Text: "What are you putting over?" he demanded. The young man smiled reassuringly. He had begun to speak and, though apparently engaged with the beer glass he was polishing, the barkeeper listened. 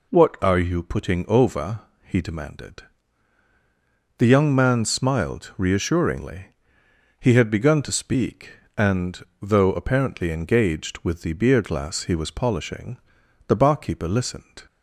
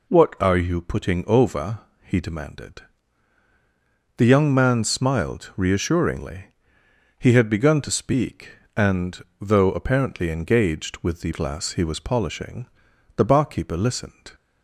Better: first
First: none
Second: skips "beer"; at 11.3 s

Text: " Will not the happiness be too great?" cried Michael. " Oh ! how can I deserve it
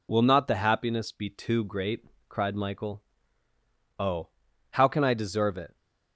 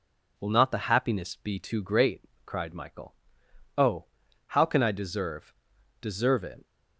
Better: first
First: none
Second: says "deserve" twice; at 5.9 s

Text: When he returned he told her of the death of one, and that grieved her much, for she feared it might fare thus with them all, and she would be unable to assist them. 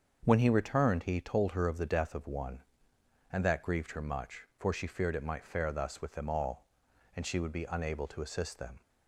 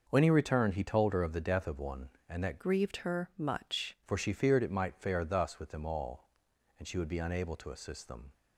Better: first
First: starts louder than the rest; until 1.2 s; 6.5 dB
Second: starts louder than the rest; noticeable; until 1.0 s; 6 dB // changes voice from "grieved" to "much"; from 2.6 to 3.9 s; 1.3 s long

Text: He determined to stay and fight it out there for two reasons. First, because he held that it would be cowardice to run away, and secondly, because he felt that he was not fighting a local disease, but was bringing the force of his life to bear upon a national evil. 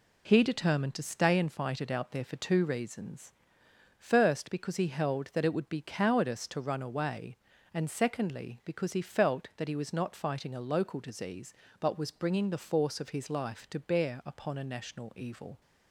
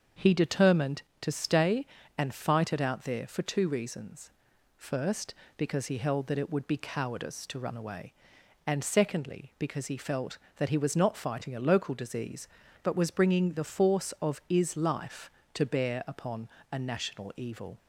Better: first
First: none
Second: starts louder than the rest; until 1.3 s; 6.5 dB // says "is" for "his"; at 14.4 s // pauses between "upon" and "a"; slight; at 16.4 s; 0.24 s long

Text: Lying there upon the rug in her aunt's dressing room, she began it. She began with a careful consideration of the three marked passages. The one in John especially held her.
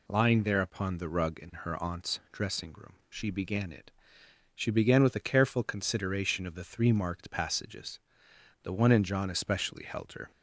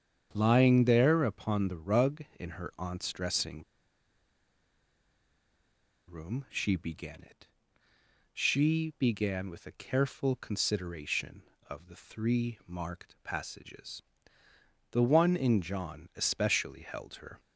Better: first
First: none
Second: starts louder than the rest; strong; until 1.3 s; 8 dB // pauses between "dressing" and "room"; strong; at 3.6 s; 2.4 s long

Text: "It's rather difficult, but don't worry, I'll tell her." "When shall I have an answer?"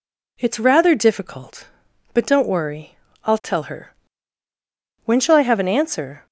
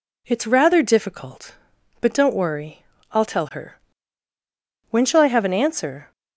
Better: neither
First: none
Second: none

